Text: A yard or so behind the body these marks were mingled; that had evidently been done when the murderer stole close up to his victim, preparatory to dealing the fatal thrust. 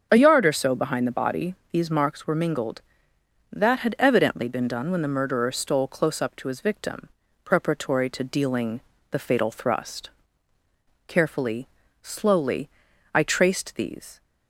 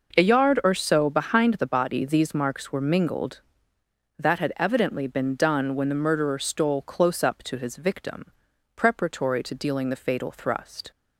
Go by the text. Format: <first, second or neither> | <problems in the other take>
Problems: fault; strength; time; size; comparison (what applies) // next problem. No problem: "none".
second | starts louder than the rest; until 1.1 s; 7 dB // pauses between "body" and "these"; slight; at 1.5 s; 0.16 s long // pauses between "dealing" and "the"; slight; at 8.7 s; 0.30 s long // goes on to say "Carefully slowly I traced these"; strong; from 11.0 s on; 3.1 s long